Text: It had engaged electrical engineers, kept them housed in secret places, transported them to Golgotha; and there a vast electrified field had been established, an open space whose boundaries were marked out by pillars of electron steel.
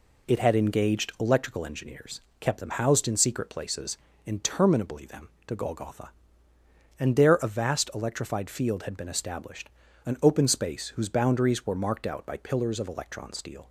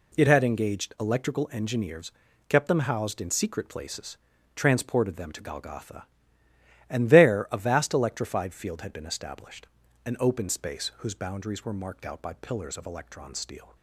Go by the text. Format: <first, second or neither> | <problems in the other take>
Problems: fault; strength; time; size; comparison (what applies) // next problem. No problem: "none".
second | says "interminably" for "transported"; at 4.2 s